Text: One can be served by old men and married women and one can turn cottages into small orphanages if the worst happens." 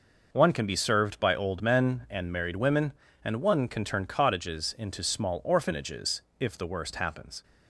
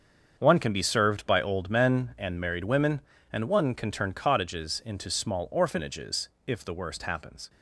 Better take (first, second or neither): first